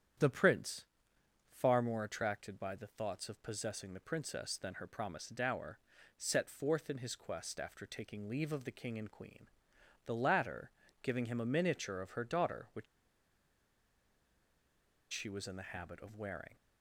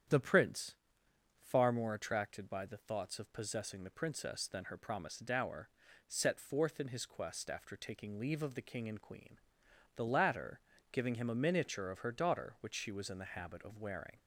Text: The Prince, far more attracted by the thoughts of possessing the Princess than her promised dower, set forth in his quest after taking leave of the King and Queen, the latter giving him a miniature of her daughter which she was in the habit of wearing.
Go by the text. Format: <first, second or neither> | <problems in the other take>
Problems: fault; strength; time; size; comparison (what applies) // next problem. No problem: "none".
second | starts louder than the rest; strong; until 1.9 s; 9 dB; strong in the second // pauses between "latter" and "giving"; slight; at 10.7 s; 0.32 s long; slight in the second // pauses between "which" and "she"; strong; at 12.8 s; 2.2 s long